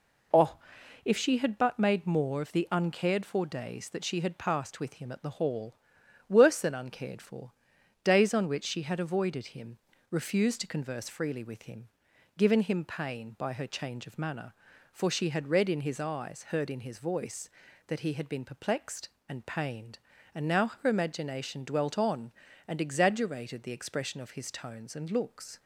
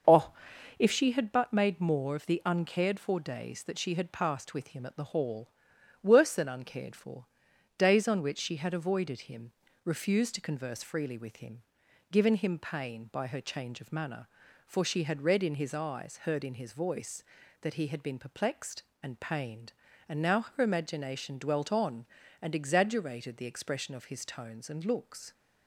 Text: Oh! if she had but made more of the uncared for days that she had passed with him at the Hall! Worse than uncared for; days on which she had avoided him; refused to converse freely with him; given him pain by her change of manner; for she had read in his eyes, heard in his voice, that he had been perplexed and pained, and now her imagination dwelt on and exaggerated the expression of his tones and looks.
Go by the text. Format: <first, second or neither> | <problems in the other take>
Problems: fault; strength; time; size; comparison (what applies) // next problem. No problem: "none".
first | starts louder than the rest; until 1.1 s; 6.5 dB